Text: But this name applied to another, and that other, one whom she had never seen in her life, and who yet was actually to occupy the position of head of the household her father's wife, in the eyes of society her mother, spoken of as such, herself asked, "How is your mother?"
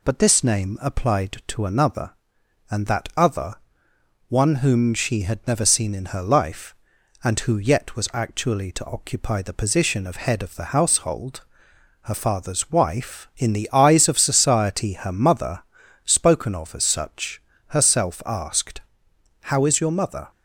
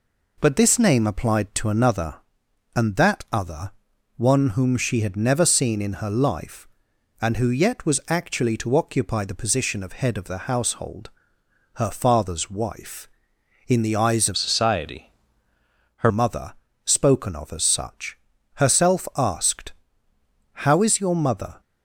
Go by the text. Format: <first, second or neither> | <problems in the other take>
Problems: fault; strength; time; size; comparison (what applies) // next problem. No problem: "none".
first | pauses between "household" and "her"; noticeable; at 11.0 s; 0.66 s long; noticeable in the first // changes voice from "society" to "her"; from 14.3 to 16.1 s; 1.8 s long // pauses between "society" and "her"; noticeable; at 15.1 s; 0.86 s long